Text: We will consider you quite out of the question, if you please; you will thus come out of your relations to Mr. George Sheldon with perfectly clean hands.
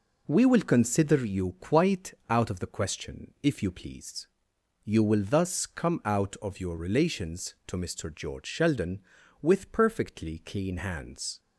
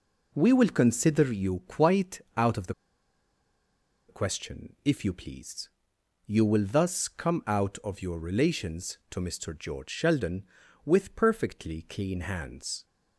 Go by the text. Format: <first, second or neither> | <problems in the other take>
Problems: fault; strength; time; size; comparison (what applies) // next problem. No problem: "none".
first | pauses between "quite" and "out"; slight; at 2.2 s; 0.18 s long; slight in the first // pauses between "the" and "question"; strong; at 2.7 s; 1.3 s long